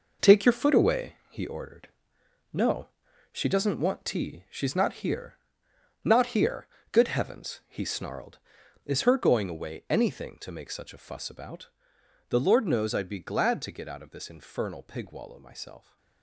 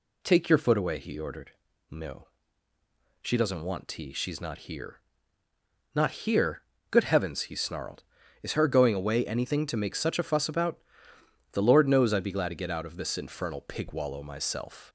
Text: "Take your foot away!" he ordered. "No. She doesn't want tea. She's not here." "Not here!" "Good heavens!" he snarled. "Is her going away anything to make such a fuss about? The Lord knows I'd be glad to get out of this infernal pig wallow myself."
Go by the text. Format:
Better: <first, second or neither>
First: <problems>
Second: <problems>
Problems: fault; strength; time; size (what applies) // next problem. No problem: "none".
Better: second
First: gets quieter; strong; throughout; 9.5 dB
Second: none